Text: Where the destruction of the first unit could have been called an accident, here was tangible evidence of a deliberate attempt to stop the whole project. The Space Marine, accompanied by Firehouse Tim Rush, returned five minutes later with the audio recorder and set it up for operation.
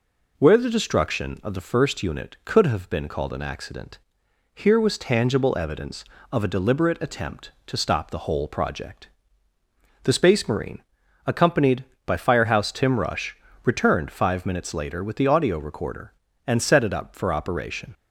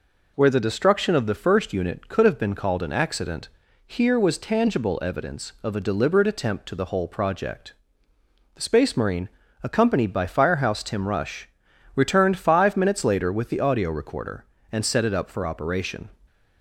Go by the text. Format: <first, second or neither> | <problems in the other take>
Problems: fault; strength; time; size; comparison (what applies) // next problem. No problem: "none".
first | skips "stop"; at 6.7 s